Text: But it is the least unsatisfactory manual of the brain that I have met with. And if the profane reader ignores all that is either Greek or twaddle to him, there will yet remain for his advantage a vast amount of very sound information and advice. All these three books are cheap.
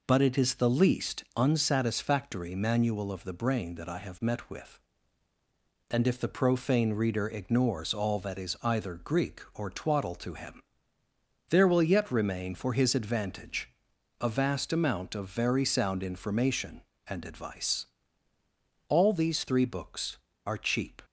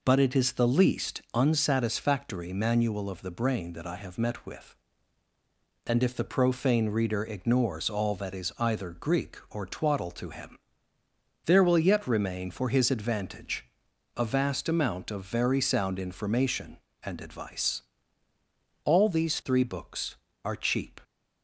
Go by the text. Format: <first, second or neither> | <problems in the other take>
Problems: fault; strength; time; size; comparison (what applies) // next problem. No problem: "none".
neither | pauses between "advantage" and "a"; noticeable; the same in both